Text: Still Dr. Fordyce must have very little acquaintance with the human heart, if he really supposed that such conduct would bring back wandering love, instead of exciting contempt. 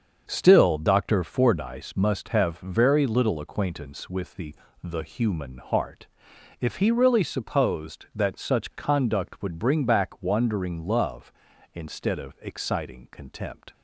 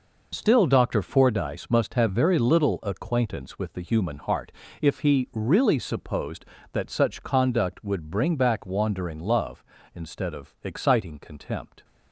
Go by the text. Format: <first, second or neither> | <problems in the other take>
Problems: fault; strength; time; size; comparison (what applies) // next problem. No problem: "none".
second | starts louder than the rest; until 1.3 s; 7 dB // says "the" twice; at 4.8 s